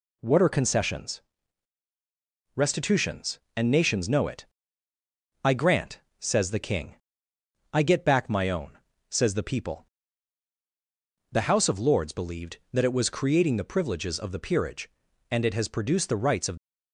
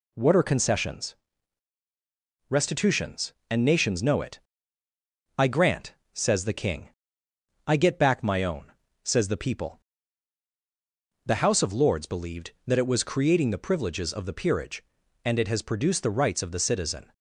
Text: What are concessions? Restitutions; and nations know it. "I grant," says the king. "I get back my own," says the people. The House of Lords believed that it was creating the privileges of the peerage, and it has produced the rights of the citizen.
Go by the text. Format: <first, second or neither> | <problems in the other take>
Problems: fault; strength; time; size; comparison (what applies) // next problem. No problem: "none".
second | stops before "the citizen"; at 16.5 s